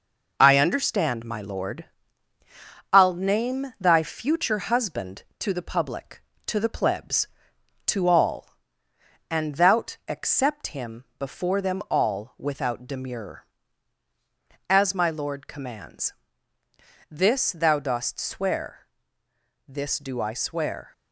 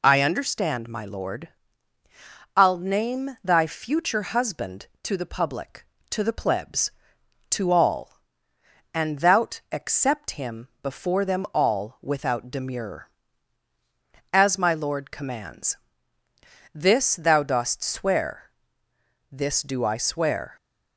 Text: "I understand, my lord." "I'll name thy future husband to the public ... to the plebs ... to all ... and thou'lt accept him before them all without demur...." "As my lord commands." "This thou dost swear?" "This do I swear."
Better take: second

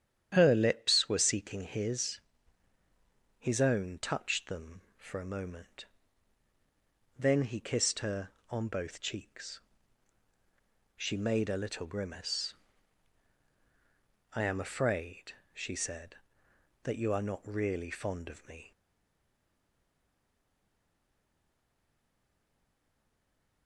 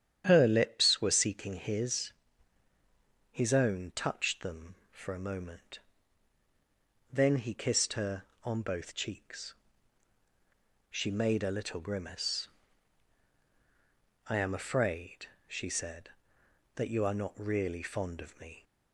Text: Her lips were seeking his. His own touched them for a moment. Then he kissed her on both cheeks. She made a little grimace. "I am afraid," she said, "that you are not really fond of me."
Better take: second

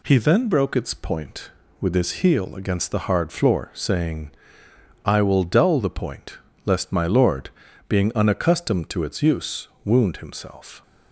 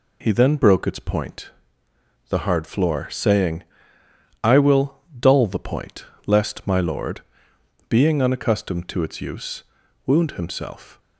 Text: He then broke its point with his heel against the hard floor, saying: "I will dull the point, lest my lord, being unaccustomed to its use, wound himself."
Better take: first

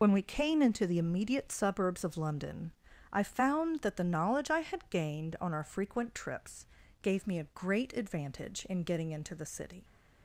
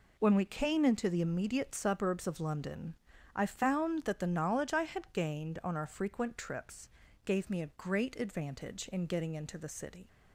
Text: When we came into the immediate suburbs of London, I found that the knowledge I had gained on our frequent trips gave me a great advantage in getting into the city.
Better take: second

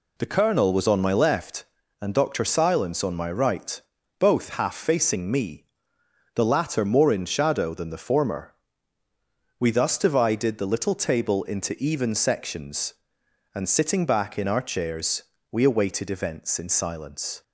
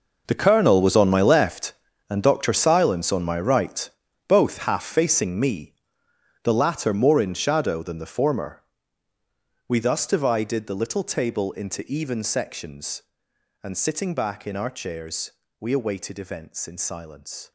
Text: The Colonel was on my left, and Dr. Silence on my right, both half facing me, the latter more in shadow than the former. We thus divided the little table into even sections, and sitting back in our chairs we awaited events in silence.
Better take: first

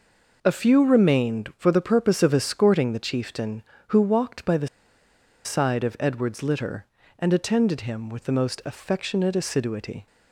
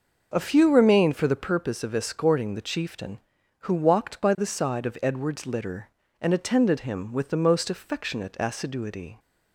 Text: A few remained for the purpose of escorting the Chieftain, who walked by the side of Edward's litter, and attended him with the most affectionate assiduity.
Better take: second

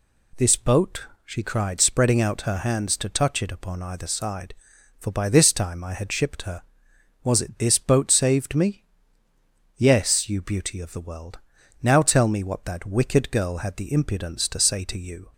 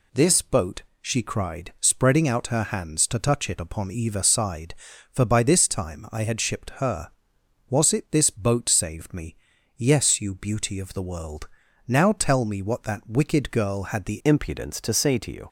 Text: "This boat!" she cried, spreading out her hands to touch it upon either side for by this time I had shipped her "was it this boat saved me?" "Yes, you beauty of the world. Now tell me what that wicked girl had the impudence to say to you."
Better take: first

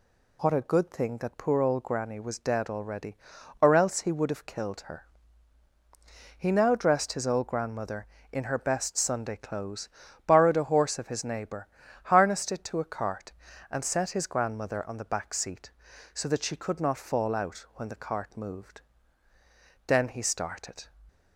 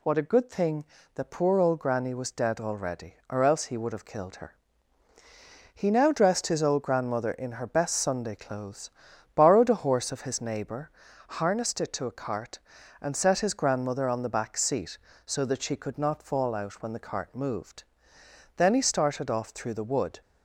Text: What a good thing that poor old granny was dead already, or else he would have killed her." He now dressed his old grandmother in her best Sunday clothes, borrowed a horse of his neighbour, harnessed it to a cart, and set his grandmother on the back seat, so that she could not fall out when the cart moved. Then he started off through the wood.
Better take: second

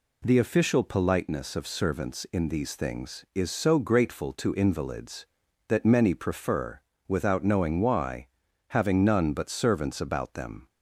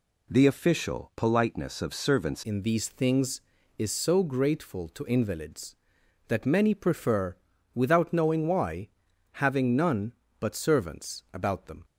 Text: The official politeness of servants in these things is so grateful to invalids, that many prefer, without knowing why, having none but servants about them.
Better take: first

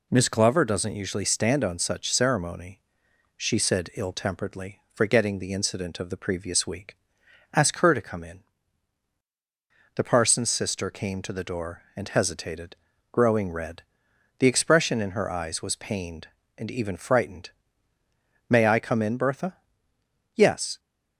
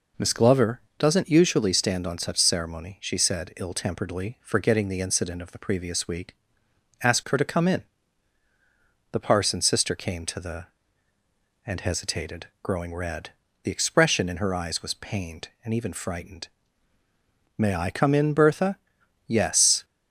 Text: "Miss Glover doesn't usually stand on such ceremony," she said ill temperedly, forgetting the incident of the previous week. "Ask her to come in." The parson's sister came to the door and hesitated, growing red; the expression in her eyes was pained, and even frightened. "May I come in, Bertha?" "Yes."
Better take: first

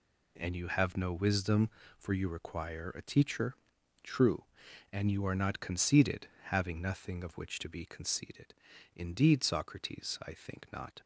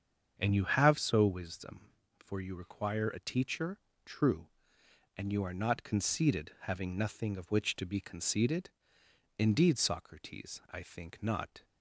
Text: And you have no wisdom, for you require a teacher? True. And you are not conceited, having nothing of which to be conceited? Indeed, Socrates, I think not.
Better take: first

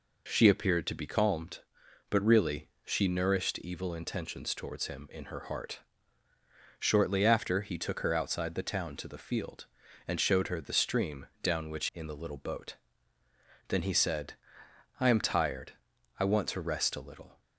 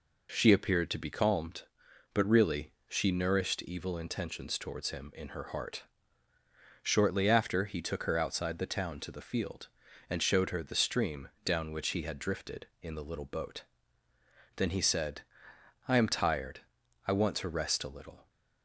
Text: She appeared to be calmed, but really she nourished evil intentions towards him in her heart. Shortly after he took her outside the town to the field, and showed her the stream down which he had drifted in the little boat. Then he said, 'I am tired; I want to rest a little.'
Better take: second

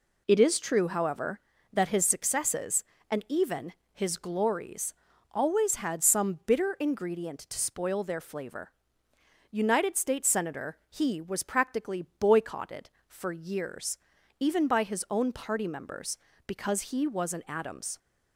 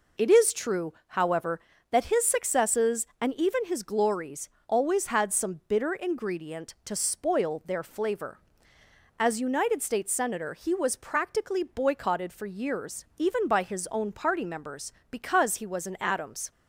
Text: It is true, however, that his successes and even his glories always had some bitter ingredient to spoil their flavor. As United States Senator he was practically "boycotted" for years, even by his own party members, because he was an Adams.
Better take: second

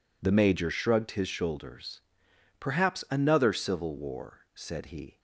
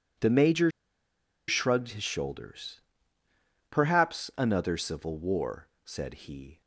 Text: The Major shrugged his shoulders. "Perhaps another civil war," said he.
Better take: first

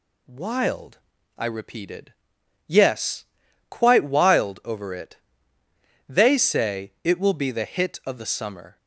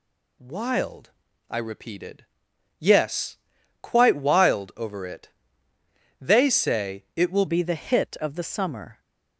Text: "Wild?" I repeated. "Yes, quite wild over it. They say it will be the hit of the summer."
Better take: first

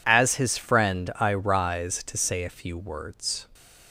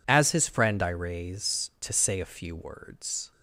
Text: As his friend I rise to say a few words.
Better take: first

